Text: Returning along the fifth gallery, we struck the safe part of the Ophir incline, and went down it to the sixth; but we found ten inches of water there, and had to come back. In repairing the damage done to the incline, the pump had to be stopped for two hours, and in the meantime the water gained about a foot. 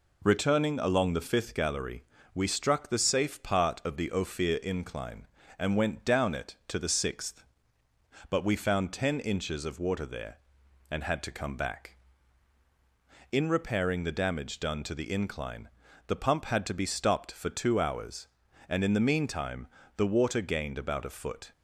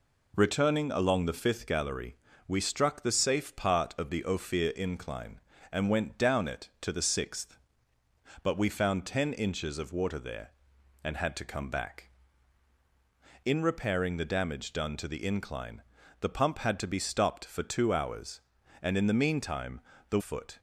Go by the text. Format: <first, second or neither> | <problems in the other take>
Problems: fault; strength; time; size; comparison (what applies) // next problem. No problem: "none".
first | pauses between "meantime" and "the"; slight; at 19.7 s; 0.30 s long; slight in the first // skips "water gained about a"; at 20.1 s